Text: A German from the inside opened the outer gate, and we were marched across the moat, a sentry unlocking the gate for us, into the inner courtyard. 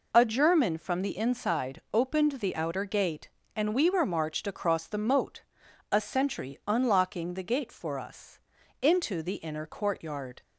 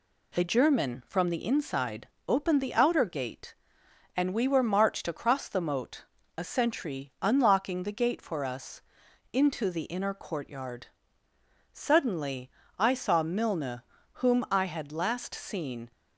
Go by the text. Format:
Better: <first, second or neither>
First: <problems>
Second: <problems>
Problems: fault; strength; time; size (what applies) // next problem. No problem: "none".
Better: first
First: none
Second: pauses between "inside" and "opened"; slight; at 2.0 s; 0.20 s long // goes on to say "Suddenly I saw Milne whom I had last seen"; strong; from 11.7 s on; 4.2 s long